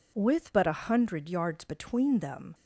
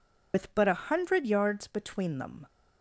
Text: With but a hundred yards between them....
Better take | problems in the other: first | loses the start of "With"; at 0.3 s; 80 ms

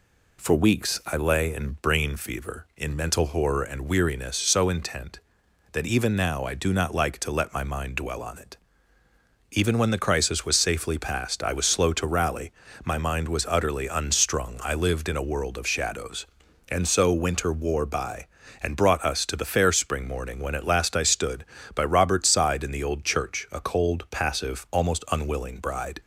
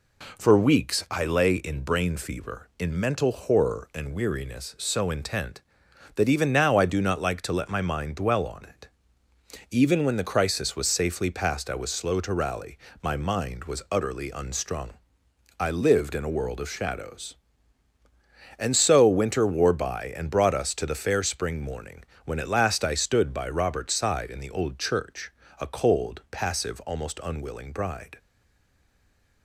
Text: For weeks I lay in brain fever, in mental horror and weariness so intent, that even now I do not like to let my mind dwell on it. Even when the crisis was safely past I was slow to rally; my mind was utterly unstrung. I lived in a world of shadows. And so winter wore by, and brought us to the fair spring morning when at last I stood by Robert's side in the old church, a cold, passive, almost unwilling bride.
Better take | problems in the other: first | pauses between "morning" and "when"; slight; at 22.0 s; 0.22 s long // stays silent after the last word; noticeable; from 28.1 s on; 1.3 s long

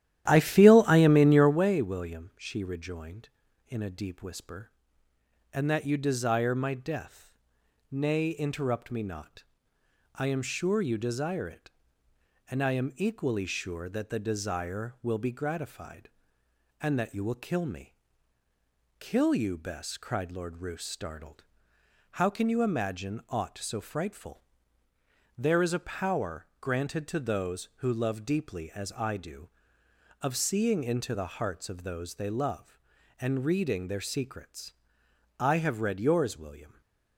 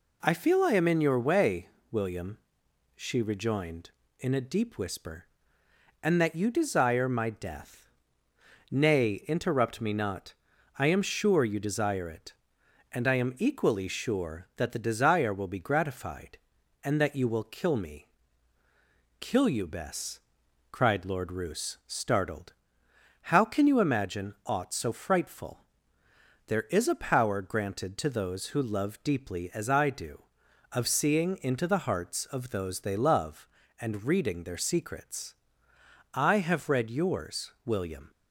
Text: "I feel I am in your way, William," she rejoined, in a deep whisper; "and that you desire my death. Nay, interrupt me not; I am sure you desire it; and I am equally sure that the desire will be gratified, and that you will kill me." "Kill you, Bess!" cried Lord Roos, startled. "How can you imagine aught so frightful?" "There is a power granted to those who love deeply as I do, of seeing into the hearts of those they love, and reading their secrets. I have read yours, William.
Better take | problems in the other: second | starts louder than the rest; strong; until 1.7 s; 12.5 dB // stays silent after the last word; slight; from 36.6 s on; 0.5 s long

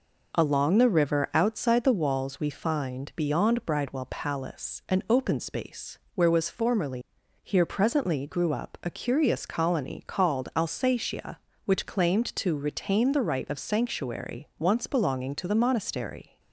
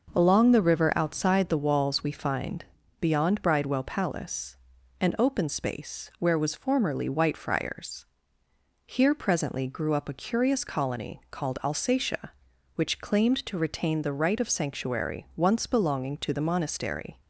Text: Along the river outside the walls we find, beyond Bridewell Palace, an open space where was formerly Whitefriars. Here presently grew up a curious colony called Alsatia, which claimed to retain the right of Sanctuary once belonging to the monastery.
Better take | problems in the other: second | pauses between "space" and "where"; slight; at 5.9 s; 0.16 s long // skips "Whitefriars"; at 7.2 s

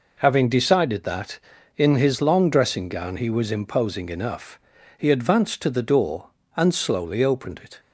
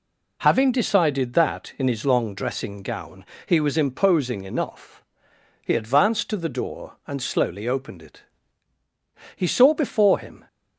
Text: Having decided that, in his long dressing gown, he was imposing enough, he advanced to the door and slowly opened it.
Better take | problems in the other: first | goes on to say "He saw before him"; noticeable; from 9.3 s on; 1.1 s long

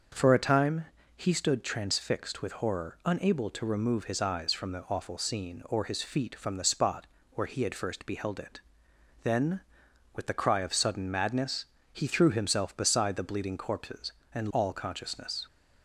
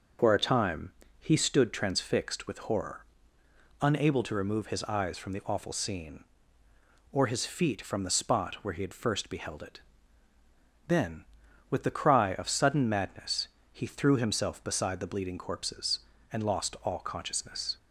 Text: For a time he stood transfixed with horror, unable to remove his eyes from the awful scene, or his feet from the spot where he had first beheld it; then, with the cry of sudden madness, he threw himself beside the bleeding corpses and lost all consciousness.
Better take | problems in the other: second | starts louder than the rest; until 1.4 s; 6 dB // pauses between "time" and "he"; slight; at 0.8 s; 0.32 s long; slight in the second // pauses between "spot" and "where"; slight; at 7.0 s; 0.26 s long // skips "lost"; at 14.5 s

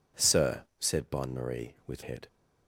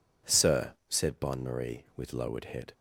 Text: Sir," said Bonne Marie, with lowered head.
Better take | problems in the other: second | skips "lowered"; at 2.0 s

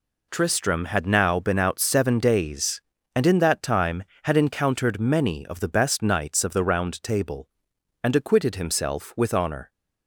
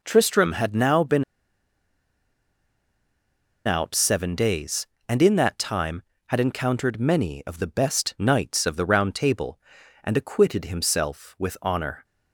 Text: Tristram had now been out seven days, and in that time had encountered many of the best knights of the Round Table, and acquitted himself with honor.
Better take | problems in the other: first | pauses between "been" and "out"; strong; at 1.2 s; 2.4 s long

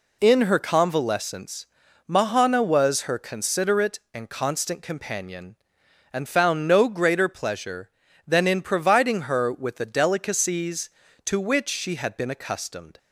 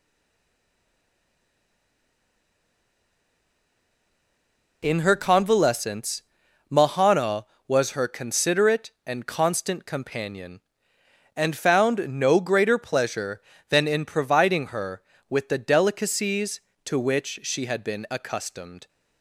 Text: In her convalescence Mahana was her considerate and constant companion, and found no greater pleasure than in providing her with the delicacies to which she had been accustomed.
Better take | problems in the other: first | stays silent before the first word; strong; until 4.8 s; 4.8 s long // pauses between "convalescence" and "Mahana"; noticeable; at 6.2 s; 0.48 s long; also in the first

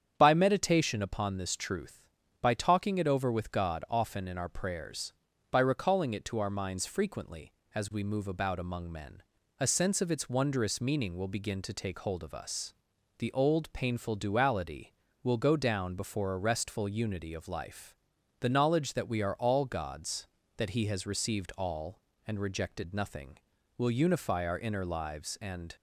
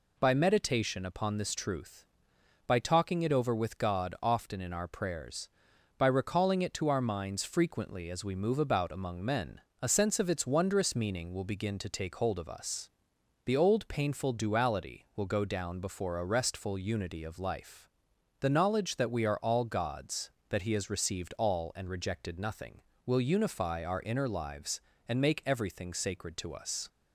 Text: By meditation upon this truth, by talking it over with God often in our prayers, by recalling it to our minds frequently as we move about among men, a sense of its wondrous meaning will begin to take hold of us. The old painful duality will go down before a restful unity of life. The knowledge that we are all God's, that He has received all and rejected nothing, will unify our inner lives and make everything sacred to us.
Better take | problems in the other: second | starts louder than the rest; strong; until 1.1 s; 8.5 dB // stops before "make everything sacred to us"; at 25.7 s

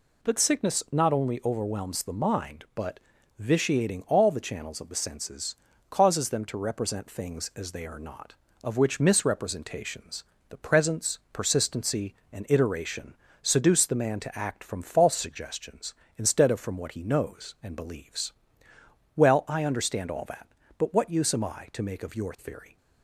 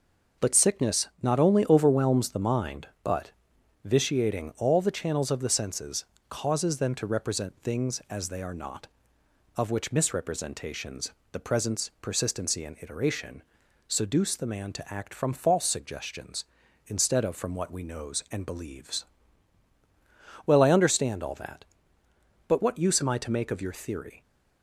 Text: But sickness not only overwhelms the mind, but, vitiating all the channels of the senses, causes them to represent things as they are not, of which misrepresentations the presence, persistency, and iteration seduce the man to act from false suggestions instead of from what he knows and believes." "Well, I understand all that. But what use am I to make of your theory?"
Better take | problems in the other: first | pauses between "misrepresentations" and "the"; slight; at 11.1 s; 0.20 s long; slight in the first // pauses between "iteration" and "seduce"; noticeable; at 13.4 s; 0.46 s long; slight in the first // says "we" for "he"; at 17.7 s

